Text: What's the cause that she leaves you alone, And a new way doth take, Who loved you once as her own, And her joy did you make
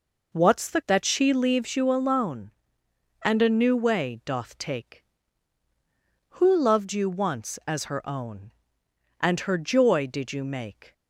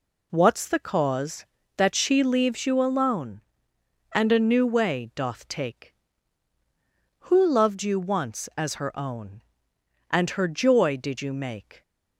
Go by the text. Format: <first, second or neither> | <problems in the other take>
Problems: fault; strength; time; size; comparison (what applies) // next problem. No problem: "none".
second | skips "cause"; at 0.8 s